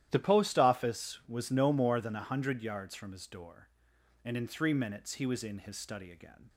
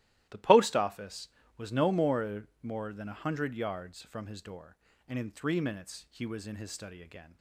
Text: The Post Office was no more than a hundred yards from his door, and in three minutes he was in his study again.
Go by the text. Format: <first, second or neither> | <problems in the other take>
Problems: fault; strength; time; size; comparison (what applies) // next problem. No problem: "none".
first | starts louder than the rest; strong; until 1.5 s; 15 dB; strong in the first // says "more" twice; at 2.6 s